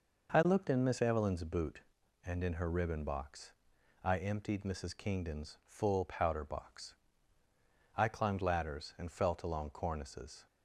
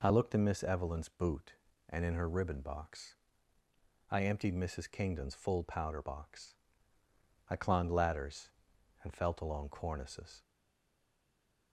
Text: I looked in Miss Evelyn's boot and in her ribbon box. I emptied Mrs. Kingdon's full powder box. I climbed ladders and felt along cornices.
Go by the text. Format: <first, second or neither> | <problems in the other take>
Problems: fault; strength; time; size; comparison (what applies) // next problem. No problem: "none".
first | stays silent after the last word; noticeable; from 10.4 s on; 1.3 s long